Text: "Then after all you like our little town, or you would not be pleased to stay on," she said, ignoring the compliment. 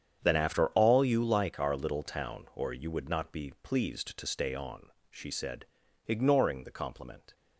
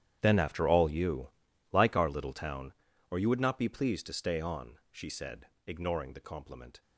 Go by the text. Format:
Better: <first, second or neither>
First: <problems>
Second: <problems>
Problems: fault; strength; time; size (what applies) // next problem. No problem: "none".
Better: first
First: starts louder than the rest; strong; until 1.2 s; 8 dB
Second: gets quieter; strong; throughout; 17.5 dB // starts louder than the rest; strong; until 1.2 s; 10.5 dB // pauses between "you" and "like"; at 1.2 s; 0.42 s long